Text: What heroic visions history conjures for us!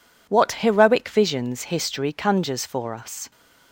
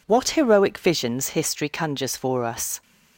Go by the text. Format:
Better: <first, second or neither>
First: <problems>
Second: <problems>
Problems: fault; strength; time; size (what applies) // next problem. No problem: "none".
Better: neither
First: none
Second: none